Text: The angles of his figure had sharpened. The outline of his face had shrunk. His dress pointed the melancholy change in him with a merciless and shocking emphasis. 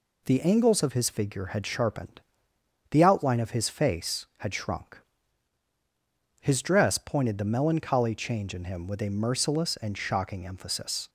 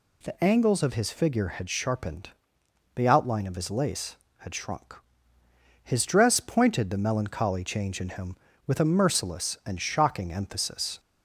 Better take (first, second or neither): first